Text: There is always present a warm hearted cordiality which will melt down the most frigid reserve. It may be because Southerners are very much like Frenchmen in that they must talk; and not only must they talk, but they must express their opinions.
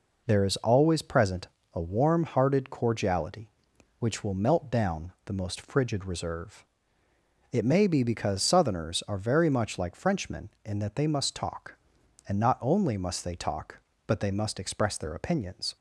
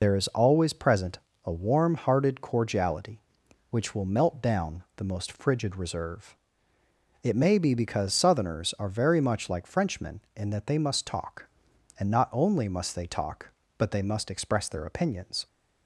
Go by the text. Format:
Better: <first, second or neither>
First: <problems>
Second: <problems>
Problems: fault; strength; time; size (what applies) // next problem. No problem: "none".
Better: first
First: pauses between "present" and "a"; slight; at 1.4 s; 0.26 s long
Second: loses the start of "There"; at 0.0 s; 50 ms // pauses between "present" and "a"; slight; at 1.1 s; 0.26 s long